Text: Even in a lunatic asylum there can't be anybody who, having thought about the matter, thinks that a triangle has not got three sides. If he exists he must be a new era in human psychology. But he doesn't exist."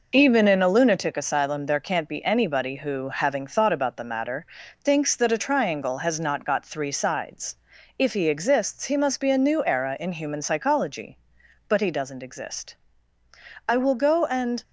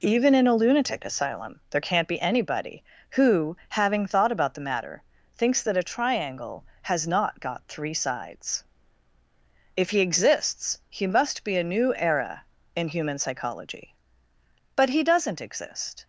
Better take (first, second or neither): second